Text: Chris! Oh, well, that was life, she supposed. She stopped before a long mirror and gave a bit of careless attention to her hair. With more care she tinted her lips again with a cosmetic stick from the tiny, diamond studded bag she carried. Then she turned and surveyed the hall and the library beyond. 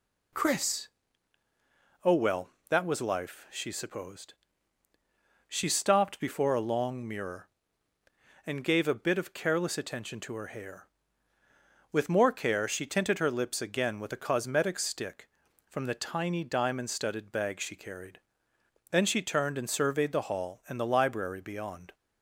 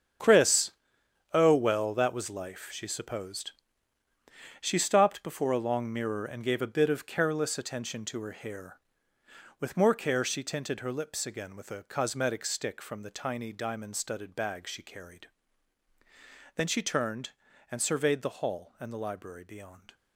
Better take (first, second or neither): first